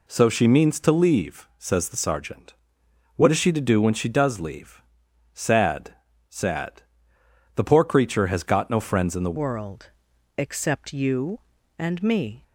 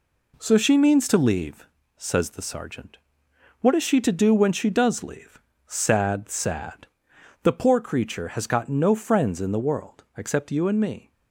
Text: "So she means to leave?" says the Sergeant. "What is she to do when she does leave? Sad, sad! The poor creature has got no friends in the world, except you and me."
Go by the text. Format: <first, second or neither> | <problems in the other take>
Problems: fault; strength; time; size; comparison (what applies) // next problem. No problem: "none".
second | changes voice at "world"; from 9.3 s on; 3.1 s long